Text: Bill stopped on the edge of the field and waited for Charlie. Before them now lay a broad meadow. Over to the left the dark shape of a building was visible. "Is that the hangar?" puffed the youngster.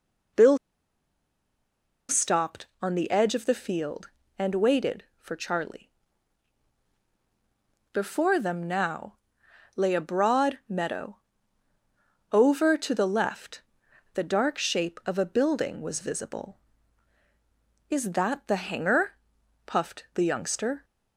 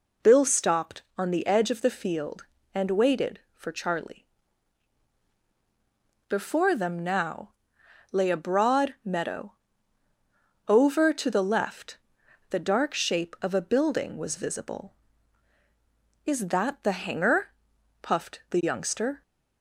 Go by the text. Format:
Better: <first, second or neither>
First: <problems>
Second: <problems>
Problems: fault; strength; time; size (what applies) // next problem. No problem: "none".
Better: second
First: pauses between "Bill" and "stopped"; strong; at 0.5 s; 1.5 s long // pauses between "now" and "lay"; noticeable; at 9.1 s; 0.60 s long // pauses between "left" and "the"; noticeable; at 13.6 s; 0.52 s long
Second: pauses between "now" and "lay"; noticeable; at 7.5 s; 0.60 s long // pauses between "left" and "the"; noticeable; at 11.9 s; 0.52 s long